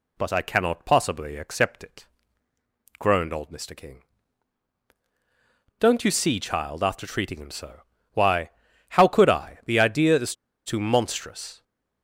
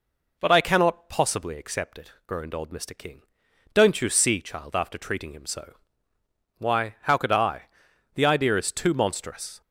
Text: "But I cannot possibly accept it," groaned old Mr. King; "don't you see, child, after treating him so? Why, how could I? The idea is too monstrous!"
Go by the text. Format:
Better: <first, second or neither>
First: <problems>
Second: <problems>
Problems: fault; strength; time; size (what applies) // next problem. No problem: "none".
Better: second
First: pauses between "is" and "too"; slight; at 10.3 s; 0.31 s long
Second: none